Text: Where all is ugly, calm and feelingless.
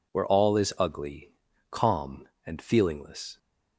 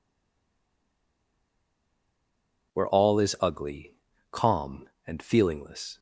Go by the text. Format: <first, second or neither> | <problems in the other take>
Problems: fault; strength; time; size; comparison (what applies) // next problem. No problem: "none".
first | stays silent before the first word; strong; until 2.7 s; 2.7 s long